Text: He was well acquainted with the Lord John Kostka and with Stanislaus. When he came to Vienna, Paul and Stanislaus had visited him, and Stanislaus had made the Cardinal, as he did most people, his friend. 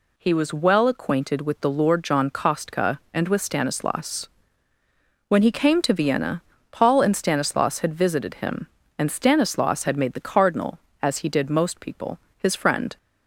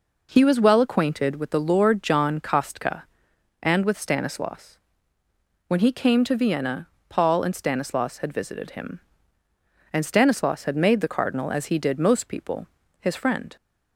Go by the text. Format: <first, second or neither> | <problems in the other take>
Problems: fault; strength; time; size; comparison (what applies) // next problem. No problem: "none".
neither | none